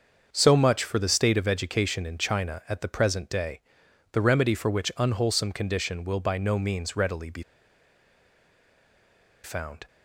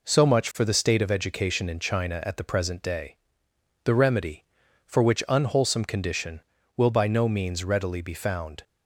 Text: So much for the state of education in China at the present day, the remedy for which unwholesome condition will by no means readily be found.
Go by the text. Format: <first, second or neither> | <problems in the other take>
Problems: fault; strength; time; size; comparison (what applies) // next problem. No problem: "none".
second | starts louder than the rest; until 1.3 s; 6.5 dB // pauses between "be" and "found"; strong; at 7.4 s; 2.0 s long